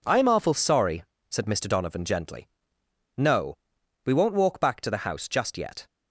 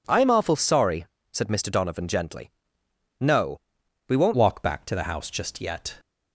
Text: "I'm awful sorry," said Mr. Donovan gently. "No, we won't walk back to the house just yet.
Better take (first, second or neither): first